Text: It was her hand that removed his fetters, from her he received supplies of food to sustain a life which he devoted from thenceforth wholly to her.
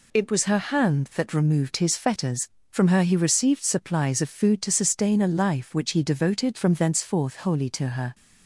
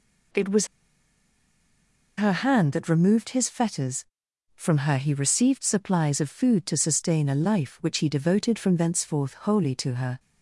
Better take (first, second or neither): first